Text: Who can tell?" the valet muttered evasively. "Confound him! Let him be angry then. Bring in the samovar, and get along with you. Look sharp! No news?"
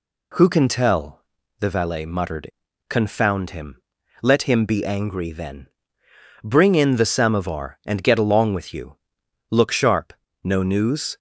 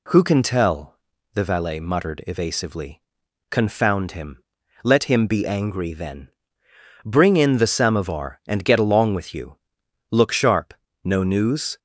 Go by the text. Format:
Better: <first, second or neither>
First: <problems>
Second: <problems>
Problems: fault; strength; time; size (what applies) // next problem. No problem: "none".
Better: second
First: skips "evasively"; at 2.6 s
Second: none